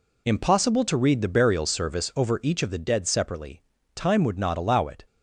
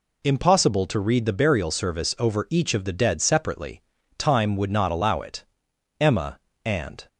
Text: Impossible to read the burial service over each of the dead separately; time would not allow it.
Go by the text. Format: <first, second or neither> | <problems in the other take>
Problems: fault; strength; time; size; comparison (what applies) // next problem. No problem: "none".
first | goes on to say "Emma and"; noticeable; from 6.0 s on; 1.0 s long